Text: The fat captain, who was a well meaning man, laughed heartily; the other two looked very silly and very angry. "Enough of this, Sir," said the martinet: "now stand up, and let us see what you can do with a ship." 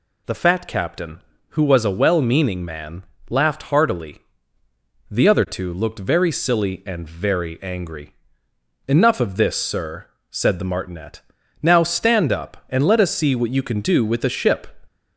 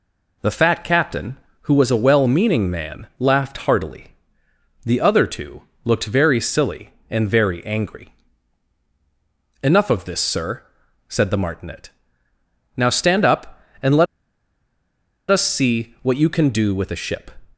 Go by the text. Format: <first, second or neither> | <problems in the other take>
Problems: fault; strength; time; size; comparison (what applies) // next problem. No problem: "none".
first | pauses between "two" and "looked"; slight; at 5.6 s; 0.18 s long // pauses between "let" and "us"; strong; at 14.0 s; 1.2 s long